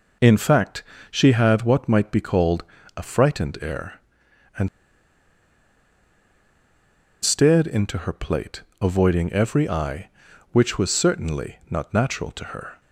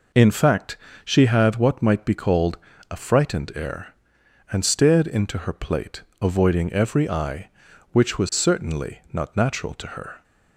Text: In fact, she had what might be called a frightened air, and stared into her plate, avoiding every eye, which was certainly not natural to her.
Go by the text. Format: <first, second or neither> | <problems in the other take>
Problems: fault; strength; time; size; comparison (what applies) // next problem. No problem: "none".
second | pauses between "called" and "a"; slight; at 2.6 s; 0.32 s long; slight in the second // pauses between "and" and "stared"; strong; at 4.6 s; 2.5 s long